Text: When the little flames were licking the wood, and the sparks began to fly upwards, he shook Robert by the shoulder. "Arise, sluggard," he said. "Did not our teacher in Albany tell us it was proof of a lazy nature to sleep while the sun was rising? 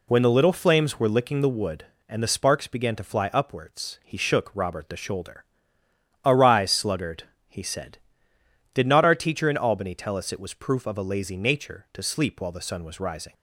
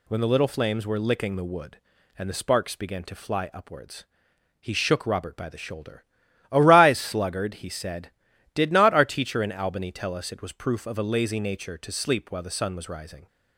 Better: second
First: skips "by"; at 4.8 s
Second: none

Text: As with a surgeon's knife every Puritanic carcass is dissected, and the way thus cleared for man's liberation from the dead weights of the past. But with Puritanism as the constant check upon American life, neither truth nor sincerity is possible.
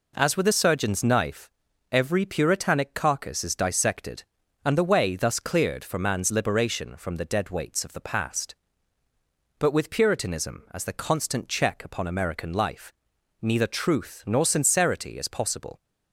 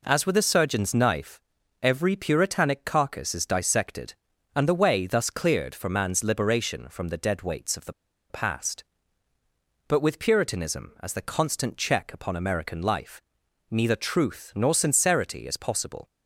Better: first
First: pauses between "knife" and "every"; at 1.4 s; 0.42 s long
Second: pauses between "knife" and "every"; at 1.3 s; 0.42 s long // pauses between "the" and "past"; at 7.9 s; 0.38 s long

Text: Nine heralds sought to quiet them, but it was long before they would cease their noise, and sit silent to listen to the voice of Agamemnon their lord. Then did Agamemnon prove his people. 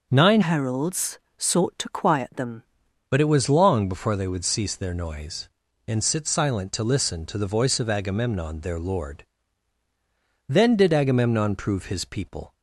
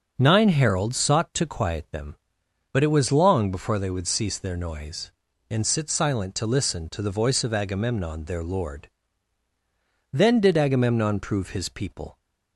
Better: second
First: starts louder than the rest; noticeable; until 1.1 s; 6 dB // changes voice from "heralds" to "them"; from 0.4 to 2.6 s; 2.2 s long // pauses between "heralds" and "sought"; slight; at 1.1 s; 0.18 s long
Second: starts louder than the rest; until 1.1 s; 6.5 dB

